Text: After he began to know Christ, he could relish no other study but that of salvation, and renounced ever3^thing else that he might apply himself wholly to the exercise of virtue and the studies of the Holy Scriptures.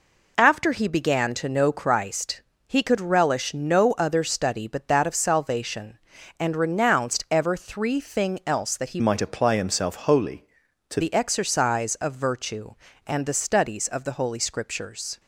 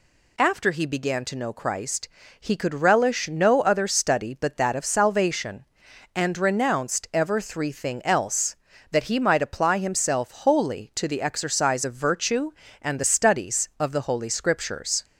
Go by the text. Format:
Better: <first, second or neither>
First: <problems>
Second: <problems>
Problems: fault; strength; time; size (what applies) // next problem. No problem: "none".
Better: second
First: changes voice from "might" to "to"; from 9.0 to 11.0 s; 2.0 s long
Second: none